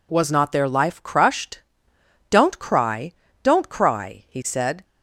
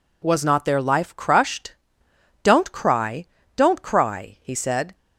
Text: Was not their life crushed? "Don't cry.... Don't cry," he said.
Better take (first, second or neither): neither